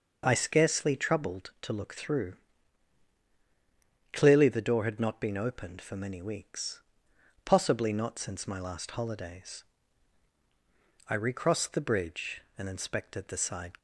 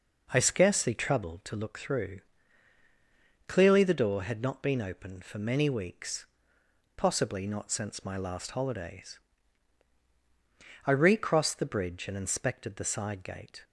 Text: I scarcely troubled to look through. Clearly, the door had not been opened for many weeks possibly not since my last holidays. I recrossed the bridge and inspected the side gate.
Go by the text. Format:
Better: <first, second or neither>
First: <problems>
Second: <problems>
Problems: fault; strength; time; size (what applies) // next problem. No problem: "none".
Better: second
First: pauses between "weeks" and "possibly"; noticeable; at 6.8 s; 0.64 s long // stops before "gate"; at 13.7 s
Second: pauses between "weeks" and "possibly"; noticeable; at 6.2 s; 0.72 s long